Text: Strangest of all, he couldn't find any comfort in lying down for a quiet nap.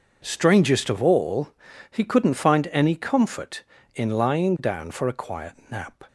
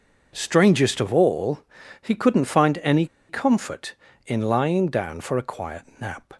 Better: first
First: pauses between "quiet" and "nap"; slight; at 5.5 s; 0.16 s long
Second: pauses between "any" and "comfort"; slight; at 3.0 s; 0.23 s long // pauses between "quiet" and "nap"; slight; at 5.8 s; 0.16 s long

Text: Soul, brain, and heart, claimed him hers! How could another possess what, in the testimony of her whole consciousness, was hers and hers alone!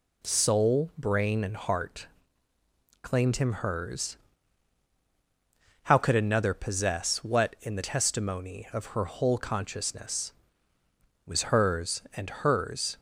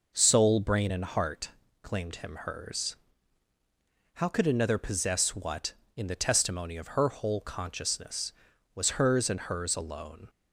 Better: second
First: stops before "alone"; at 12.9 s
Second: none

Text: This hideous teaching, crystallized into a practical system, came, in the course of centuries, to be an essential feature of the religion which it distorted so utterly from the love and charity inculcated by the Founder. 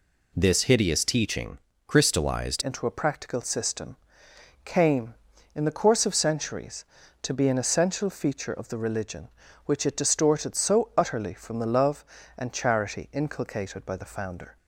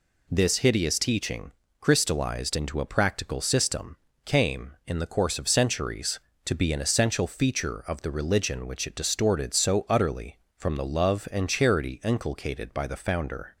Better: second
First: changes voice at "into"; from 2.6 s on; 11.9 s long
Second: none

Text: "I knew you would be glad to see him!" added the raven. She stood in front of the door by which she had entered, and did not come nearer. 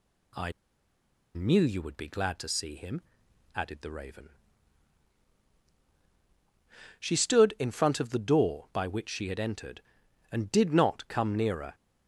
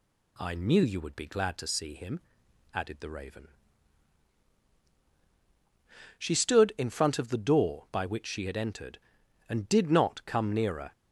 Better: second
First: pauses between "I" and "knew"; noticeable; at 0.4 s; 0.84 s long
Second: none

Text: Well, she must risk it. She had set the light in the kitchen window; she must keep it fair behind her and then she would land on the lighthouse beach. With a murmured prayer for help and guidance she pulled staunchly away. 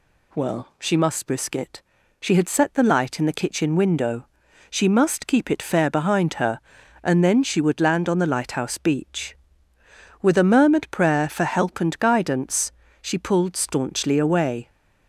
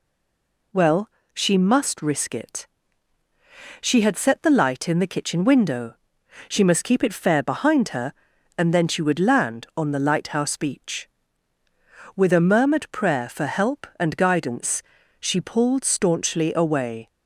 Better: first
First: pauses between "guidance" and "she"; slight; at 12.7 s; 0.30 s long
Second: stays silent before the first word; slight; until 0.7 s; 0.7 s long // pauses between "guidance" and "she"; at 14.8 s; 0.38 s long

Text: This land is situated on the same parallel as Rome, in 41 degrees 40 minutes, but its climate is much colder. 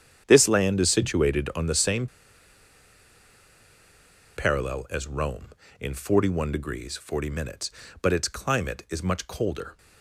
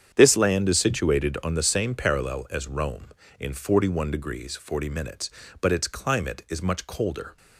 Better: second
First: starts louder than the rest; strong; until 1.2 s; 8.5 dB // pauses between "same" and "parallel"; strong; at 2.0 s; 2.3 s long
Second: starts louder than the rest; strong; until 1.1 s; 8 dB

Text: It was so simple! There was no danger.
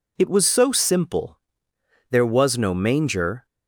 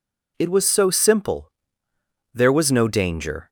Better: second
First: says "manger" for "danger"; at 2.7 s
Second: none

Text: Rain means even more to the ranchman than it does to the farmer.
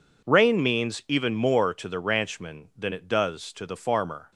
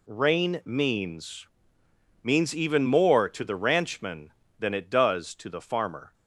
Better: first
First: none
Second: says "means" twice; at 2.2 s

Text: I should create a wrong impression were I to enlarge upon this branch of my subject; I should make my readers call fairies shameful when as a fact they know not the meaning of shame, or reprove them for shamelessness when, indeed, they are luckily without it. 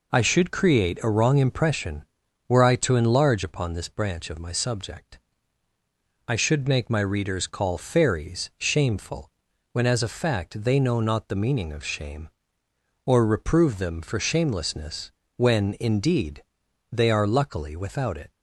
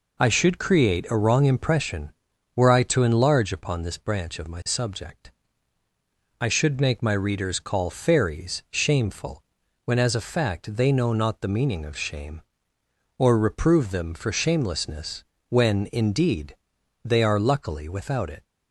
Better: neither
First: pauses between "shameful" and "when"; at 9.2 s; 0.44 s long // pauses between "shamelessness" and "when"; slight; at 15.1 s; 0.26 s long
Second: pauses between "shameful" and "when"; at 9.4 s; 0.44 s long // pauses between "shamelessness" and "when"; slight; at 15.2 s; 0.26 s long

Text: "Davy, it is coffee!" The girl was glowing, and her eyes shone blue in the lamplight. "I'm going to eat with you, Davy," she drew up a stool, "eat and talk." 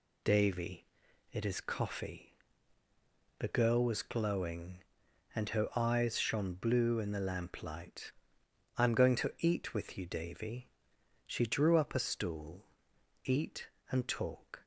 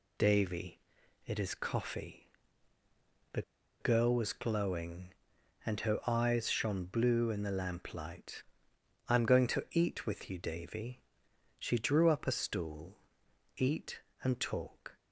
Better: first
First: none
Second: pauses between "The" and "girl"; at 3.4 s; 0.39 s long

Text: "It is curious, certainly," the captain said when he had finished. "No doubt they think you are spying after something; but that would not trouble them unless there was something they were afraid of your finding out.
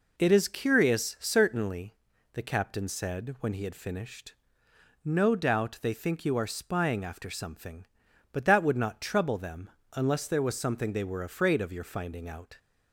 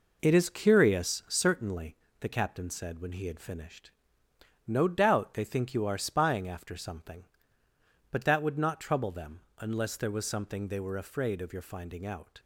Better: first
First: pauses between "them" and "unless"; slight; at 9.7 s; 0.24 s long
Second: gets quieter; noticeable; throughout; 6 dB // pauses between "them" and "unless"; slight; at 9.3 s; 0.20 s long

